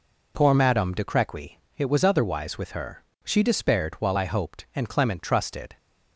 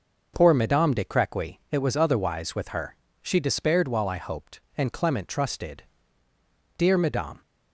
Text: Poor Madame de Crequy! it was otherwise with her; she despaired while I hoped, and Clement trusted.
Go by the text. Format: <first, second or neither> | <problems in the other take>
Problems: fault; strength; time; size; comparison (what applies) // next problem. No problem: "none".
first | goes on to say "Dear Madame"; noticeable; from 6.7 s on; 0.62 s long